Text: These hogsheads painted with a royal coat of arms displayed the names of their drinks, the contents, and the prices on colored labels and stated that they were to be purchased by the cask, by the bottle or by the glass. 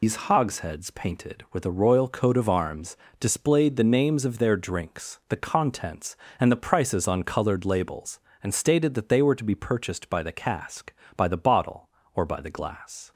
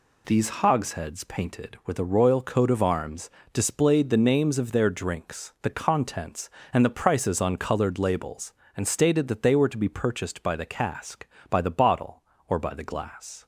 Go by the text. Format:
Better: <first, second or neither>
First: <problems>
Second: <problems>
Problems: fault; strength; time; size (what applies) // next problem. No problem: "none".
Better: second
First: loses the start of "These"; at 0.0 s; 105 ms // pauses between "arms" and "displayed"; slight; at 2.9 s; 0.24 s long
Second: pauses between "arms" and "displayed"; slight; at 3.2 s; 0.24 s long